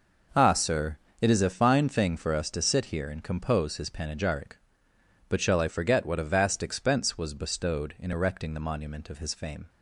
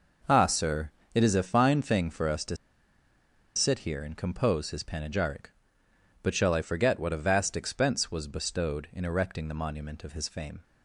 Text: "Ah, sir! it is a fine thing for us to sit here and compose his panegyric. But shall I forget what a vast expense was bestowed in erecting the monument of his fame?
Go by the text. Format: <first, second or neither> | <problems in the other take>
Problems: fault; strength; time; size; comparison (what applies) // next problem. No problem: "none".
first | pauses between "to" and "sit"; at 2.5 s; 1.0 s long